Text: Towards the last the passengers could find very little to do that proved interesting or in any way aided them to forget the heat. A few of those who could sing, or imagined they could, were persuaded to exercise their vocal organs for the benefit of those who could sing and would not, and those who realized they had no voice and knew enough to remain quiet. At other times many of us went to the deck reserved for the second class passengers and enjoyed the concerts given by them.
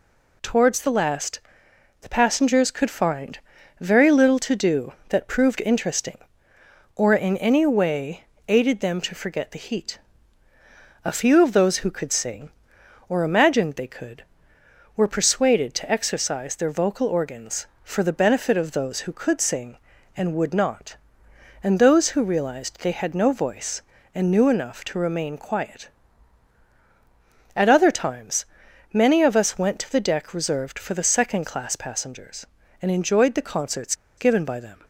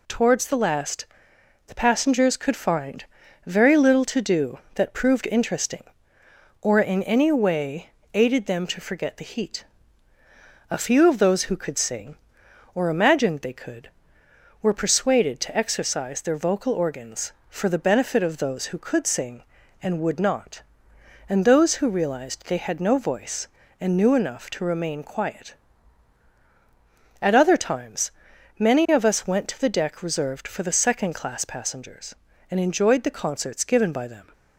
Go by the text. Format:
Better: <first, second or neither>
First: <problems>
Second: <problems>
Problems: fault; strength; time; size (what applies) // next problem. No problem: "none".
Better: second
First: pauses between "last" and "the"; noticeable; at 1.3 s; 0.62 s long // pauses between "find" and "very"; at 3.3 s; 0.40 s long // pauses between "way" and "aided"; slight; at 8.2 s; 0.24 s long // pauses between "times" and "many"; noticeable; at 28.4 s; 0.46 s long // pauses between "concerts" and "given"; slight; at 33.9 s; 0.24 s long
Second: pauses between "last" and "the"; noticeable; at 1.0 s; 0.62 s long // pauses between "find" and "very"; at 3.0 s; 0.40 s long // pauses between "way" and "aided"; slight; at 7.8 s; 0.24 s long // pauses between "times" and "many"; noticeable; at 28.1 s; 0.46 s long